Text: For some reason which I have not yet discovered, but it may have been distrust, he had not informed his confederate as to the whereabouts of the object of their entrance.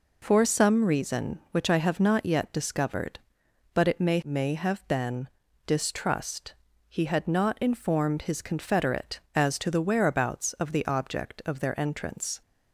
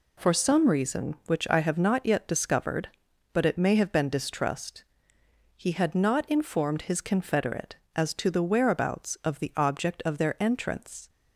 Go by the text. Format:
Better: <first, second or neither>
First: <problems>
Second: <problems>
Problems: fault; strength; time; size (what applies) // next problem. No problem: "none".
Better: second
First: says "may" twice; at 4.2 s // pauses between "been" and "distrust"; slight; at 5.2 s; 0.36 s long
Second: none